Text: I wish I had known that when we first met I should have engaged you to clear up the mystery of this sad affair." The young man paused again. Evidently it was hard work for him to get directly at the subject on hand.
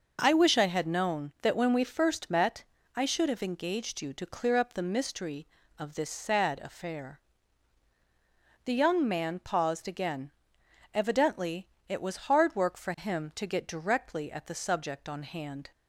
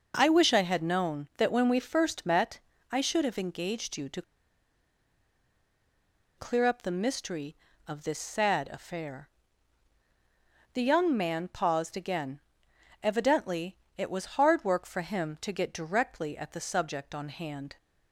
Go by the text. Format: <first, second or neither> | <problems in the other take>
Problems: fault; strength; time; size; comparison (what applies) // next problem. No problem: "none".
first | pauses between "met" and "I"; slight; at 2.5 s; 0.30 s long; slight in the first // pauses between "to" and "clear"; strong; at 4.2 s; 2.1 s long // pauses between "Evidently" and "it"; slight; at 13.7 s; 0.18 s long; slight in the first